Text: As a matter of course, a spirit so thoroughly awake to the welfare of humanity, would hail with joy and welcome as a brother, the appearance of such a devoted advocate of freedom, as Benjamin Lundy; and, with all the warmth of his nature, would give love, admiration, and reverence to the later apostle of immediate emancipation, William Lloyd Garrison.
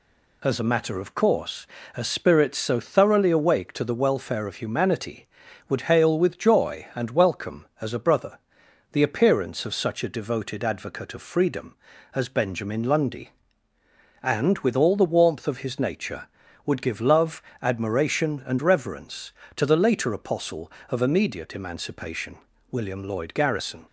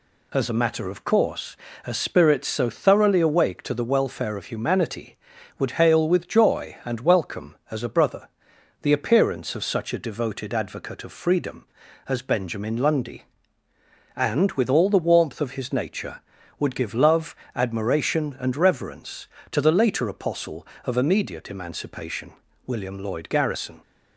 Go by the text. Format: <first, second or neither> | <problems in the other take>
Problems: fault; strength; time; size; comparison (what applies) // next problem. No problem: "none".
neither | none